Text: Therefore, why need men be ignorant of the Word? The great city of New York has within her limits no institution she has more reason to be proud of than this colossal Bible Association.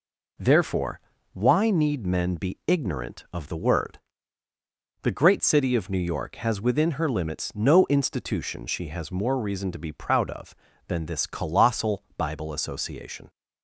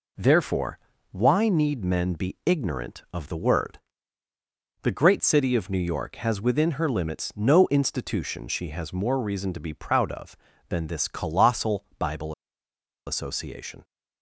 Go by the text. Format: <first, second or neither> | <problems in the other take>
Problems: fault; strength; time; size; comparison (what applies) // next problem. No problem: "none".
first | pauses between "colossal" and "Bible"; slight; at 11.8 s; 0.16 s long; slight in the first // pauses between "Bible" and "Association"; noticeable; at 12.3 s; 0.73 s long